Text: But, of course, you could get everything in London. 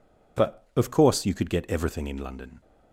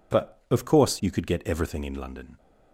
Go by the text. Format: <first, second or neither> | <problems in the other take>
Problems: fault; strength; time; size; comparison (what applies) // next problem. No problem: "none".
neither | none